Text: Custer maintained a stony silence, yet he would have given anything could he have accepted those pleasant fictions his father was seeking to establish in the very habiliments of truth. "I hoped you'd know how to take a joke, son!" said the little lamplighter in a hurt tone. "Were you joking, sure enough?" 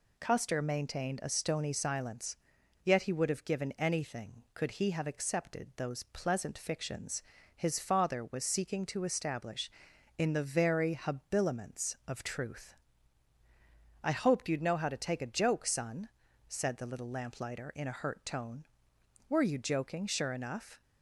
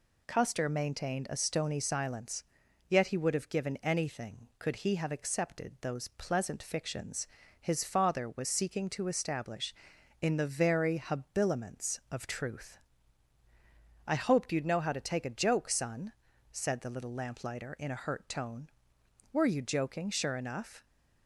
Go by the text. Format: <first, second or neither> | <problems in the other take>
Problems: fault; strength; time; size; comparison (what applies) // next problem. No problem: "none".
neither | pauses between "fictions" and "his"; slight; the same in both